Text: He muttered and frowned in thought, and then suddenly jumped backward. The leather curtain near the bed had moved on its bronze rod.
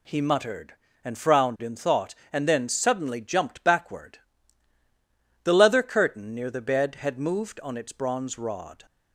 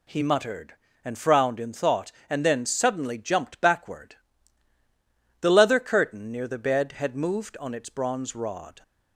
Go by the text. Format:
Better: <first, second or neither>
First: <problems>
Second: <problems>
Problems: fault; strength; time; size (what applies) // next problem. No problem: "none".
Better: neither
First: none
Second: none